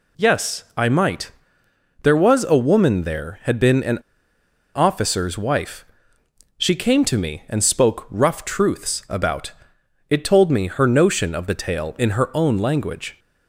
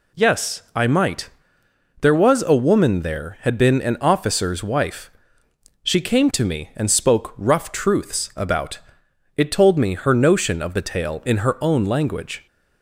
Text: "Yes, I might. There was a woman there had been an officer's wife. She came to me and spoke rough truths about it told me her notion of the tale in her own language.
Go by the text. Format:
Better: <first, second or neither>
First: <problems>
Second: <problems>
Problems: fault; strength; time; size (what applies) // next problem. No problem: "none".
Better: second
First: pauses between "an" and "officer's"; noticeable; at 3.9 s; 0.76 s long // pauses between "about" and "it"; noticeable; at 9.5 s; 0.58 s long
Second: pauses between "about" and "it"; noticeable; at 8.7 s; 0.58 s long